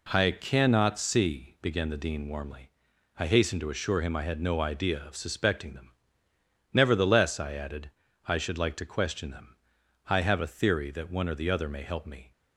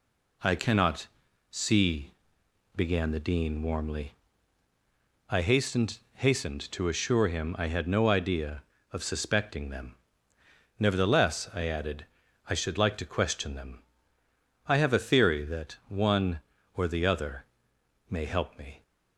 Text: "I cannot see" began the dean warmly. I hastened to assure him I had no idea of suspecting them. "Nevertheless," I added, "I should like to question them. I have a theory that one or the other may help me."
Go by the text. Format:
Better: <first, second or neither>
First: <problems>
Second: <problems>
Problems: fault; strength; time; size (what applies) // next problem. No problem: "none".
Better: first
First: none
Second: pauses between "cannot" and "see"; at 1.0 s; 0.42 s long // pauses between "see" and "began"; noticeable; at 2.1 s; 0.62 s long // says "hastened" twice; at 6.1 s // pauses between "other" and "may"; noticeable; at 17.4 s; 0.62 s long